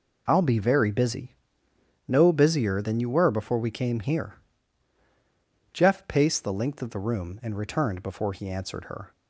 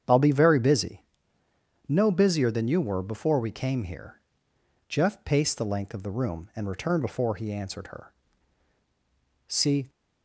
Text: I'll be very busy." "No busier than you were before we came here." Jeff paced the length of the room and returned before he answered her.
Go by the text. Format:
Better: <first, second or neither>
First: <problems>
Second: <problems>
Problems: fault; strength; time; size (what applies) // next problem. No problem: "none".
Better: first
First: none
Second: starts louder than the rest; strong; until 1.9 s; 8.5 dB // goes on to say "See"; slight; from 9.4 s on; 0.42 s long